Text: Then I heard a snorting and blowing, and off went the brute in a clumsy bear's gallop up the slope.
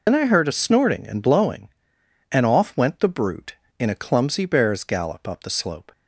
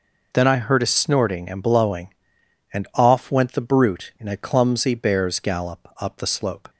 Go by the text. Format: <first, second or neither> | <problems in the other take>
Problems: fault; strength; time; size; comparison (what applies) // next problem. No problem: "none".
second | loses the start of "Then"; at 0.0 s; 65 ms